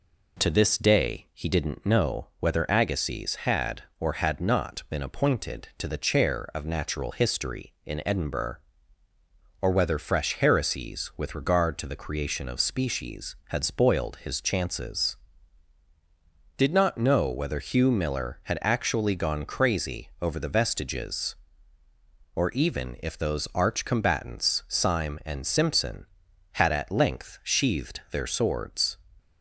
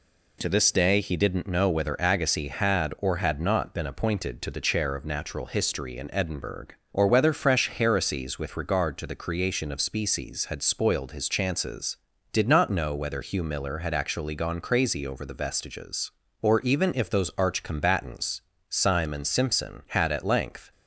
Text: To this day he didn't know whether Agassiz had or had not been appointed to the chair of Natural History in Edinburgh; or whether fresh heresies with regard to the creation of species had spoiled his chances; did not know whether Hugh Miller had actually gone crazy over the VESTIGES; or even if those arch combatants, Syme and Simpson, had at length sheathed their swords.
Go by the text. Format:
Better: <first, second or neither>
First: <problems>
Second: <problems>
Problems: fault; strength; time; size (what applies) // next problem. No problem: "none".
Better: first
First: none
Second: stops before "sheathed their swords"; at 20.7 s